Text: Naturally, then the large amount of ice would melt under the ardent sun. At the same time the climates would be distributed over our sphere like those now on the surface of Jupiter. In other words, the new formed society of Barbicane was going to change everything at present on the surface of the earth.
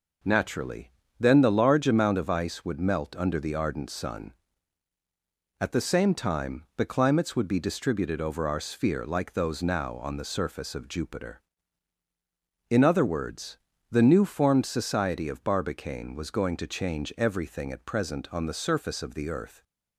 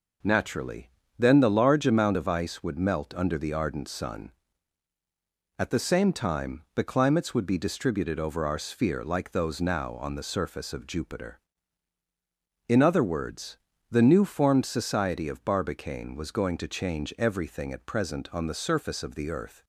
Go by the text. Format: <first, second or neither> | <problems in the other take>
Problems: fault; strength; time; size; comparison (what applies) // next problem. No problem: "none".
neither | none